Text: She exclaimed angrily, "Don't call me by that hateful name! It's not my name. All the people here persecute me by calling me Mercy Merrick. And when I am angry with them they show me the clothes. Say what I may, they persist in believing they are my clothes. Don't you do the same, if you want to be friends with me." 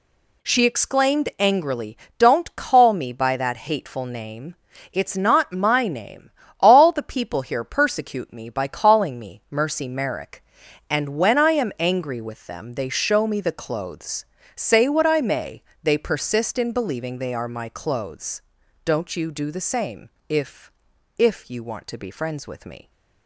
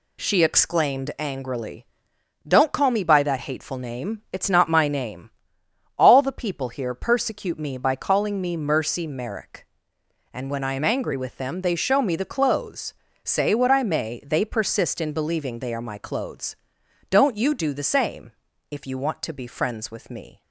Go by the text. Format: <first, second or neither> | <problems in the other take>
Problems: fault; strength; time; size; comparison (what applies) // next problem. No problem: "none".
second | says "if" twice; at 21.1 s